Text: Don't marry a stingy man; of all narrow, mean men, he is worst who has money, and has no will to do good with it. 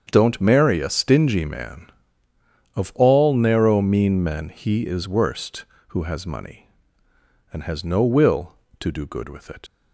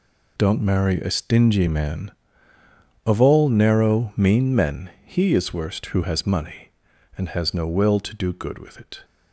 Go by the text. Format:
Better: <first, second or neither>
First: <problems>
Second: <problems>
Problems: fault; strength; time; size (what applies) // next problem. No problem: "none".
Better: second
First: starts louder than the rest; strong; until 1.1 s; 7 dB // leaves "it" unfinished; at 9.6 s; 65 ms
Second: none